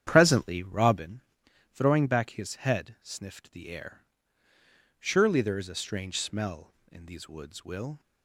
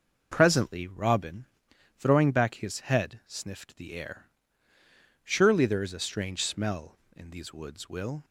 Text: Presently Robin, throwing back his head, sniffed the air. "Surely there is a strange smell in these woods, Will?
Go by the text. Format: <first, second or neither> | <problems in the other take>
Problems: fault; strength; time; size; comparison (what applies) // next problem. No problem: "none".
second | starts louder than the rest; strong; until 1.1 s; 9.5 dB